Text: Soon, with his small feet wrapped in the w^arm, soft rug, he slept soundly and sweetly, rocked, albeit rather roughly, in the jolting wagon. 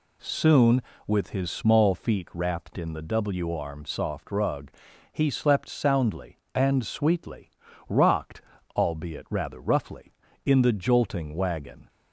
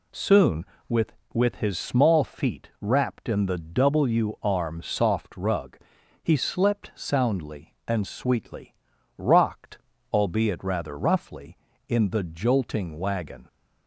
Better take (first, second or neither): first